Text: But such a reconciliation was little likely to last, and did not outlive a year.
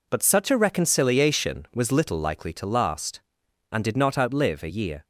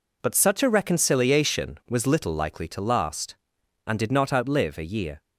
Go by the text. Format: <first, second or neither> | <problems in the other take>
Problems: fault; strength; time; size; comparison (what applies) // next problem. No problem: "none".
neither | none